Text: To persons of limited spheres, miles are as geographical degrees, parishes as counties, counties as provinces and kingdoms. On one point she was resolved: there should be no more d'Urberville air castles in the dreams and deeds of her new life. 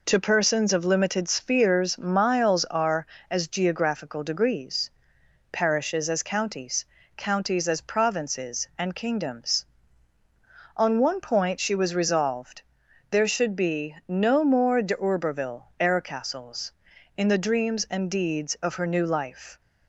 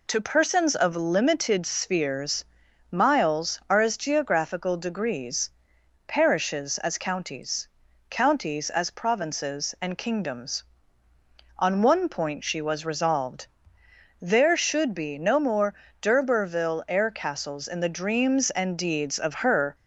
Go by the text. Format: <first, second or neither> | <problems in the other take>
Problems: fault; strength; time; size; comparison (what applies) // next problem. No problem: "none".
first | pauses between "more" and "d'Urberville"; slight; at 15.7 s; 0.30 s long // stops before "new life"; at 19.7 s